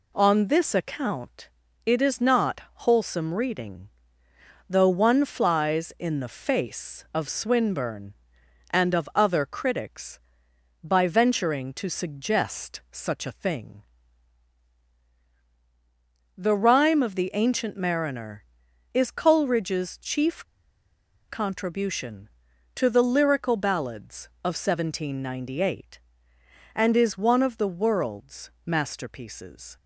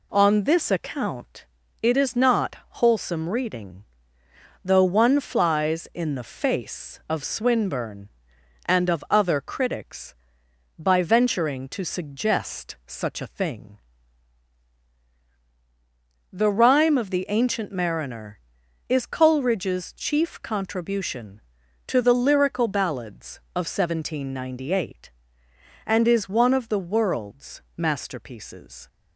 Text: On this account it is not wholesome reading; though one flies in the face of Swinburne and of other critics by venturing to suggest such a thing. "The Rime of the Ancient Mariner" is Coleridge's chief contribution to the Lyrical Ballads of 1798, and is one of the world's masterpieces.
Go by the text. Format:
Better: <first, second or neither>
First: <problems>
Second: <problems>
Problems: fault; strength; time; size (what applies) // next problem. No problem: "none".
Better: second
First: pauses between "account" and "it"; slight; at 1.4 s; 0.36 s long // pauses between "not" and "wholesome"; slight; at 2.6 s; 0.24 s long // pauses between "chief" and "contribution"; noticeable; at 20.4 s; 0.83 s long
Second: pauses between "account" and "it"; slight; at 1.4 s; 0.36 s long // pauses between "not" and "wholesome"; slight; at 2.5 s; 0.24 s long